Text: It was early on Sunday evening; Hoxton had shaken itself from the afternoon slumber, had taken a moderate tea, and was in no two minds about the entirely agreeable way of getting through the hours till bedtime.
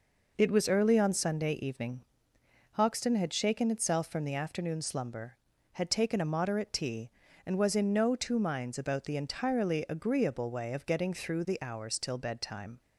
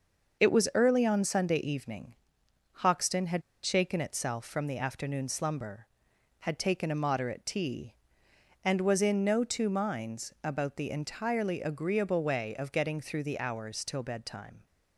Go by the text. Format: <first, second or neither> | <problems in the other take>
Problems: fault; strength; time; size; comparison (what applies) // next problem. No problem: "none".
first | starts louder than the rest; until 1.4 s; 6 dB // pauses between "had" and "shaken"; slight; at 3.4 s; 0.23 s long